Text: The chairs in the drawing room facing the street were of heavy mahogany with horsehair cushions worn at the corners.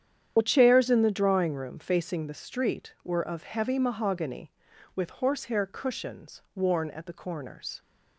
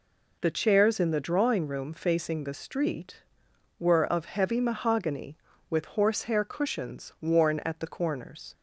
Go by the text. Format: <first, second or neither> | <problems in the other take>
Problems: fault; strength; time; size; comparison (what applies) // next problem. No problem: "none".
second | loses the start of "The"; at 0.3 s; 45 ms // starts louder than the rest; strong; until 1.3 s; 9 dB